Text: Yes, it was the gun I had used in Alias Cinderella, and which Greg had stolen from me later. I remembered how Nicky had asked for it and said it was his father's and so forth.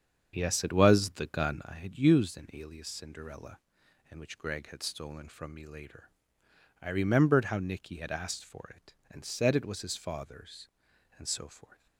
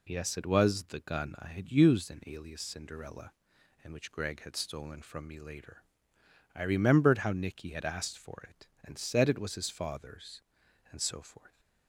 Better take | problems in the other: second | starts louder than the rest; strong; until 1.8 s; 7.5 dB

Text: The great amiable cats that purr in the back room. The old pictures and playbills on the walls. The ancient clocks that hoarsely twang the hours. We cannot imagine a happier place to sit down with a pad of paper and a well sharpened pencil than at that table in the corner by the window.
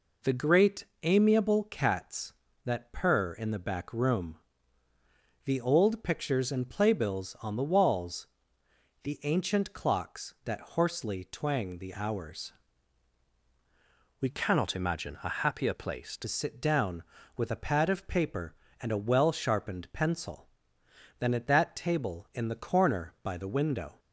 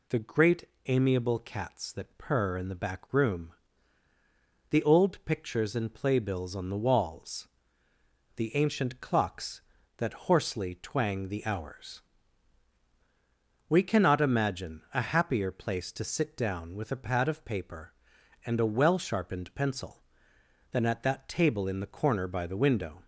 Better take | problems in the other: second | pauses between "great" and "amiable"; slight; at 0.8 s; 0.18 s long; slight in the second // changes voice from "cannot" to "to"; from 14.2 to 16.2 s; 2.0 s long

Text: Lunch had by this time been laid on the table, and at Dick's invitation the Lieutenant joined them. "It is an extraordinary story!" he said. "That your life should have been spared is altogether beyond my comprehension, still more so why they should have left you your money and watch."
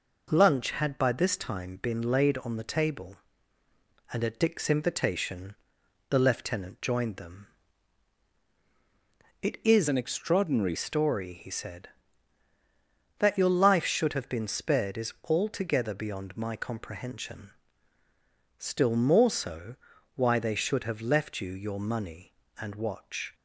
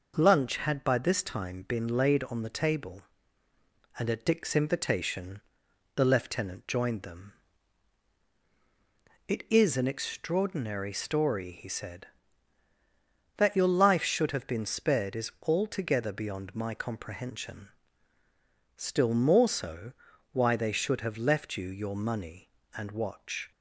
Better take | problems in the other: second | pauses between "invitation" and "the"; noticeable; at 5.5 s; 0.56 s long; noticeable in the second // changes voice from "an" to "extraordinary"; from 9.8 to 10.7 s; 0.9 s long // pauses between "so" and "why"; at 19.7 s; 0.38 s long; also in the second

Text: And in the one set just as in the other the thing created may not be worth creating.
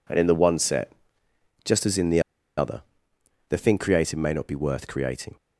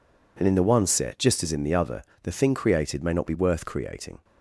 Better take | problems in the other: second | pauses between "set" and "just"; noticeable; at 0.9 s; 0.74 s long // pauses between "the" and "other"; at 2.2 s; 0.36 s long // pauses between "other" and "the"; noticeable; at 2.8 s; 0.68 s long; slight in the second

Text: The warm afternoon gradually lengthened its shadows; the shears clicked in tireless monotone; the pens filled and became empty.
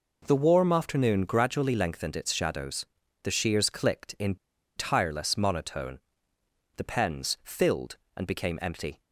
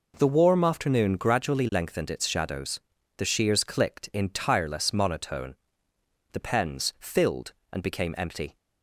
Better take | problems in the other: second | pauses between "in" and "tireless"; at 4.3 s; 0.40 s long

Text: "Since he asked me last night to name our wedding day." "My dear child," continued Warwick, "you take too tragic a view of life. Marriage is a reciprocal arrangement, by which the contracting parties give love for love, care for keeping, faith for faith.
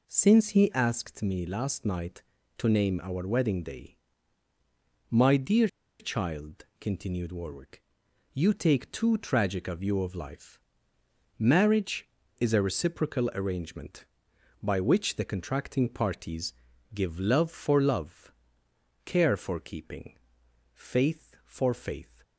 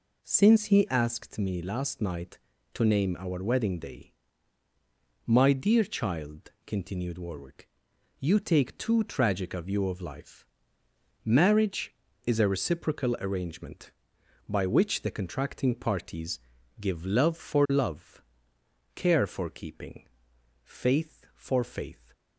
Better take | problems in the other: second | pauses between "dear" and "child"; slight; at 5.6 s; 0.32 s long // pauses between "parties" and "give"; at 16.5 s; 0.40 s long; also in the second

